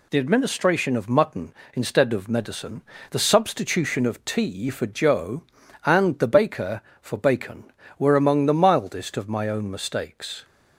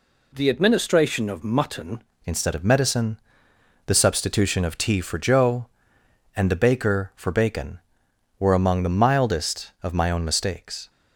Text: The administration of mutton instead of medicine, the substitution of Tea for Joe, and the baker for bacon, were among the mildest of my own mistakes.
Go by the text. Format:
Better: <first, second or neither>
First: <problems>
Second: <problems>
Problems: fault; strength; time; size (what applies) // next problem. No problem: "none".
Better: first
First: none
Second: changes voice at "instead"; from 2.2 s on; 8.6 s long